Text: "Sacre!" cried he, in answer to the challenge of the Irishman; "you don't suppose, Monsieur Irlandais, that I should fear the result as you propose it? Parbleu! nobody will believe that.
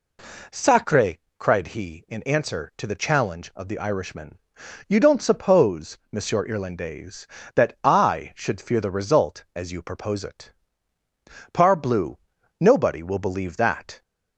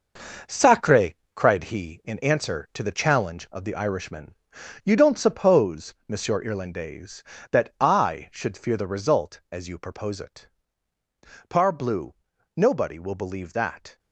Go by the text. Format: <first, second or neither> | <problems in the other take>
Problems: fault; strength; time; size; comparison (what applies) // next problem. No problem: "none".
first | gets quieter; strong; throughout; 10 dB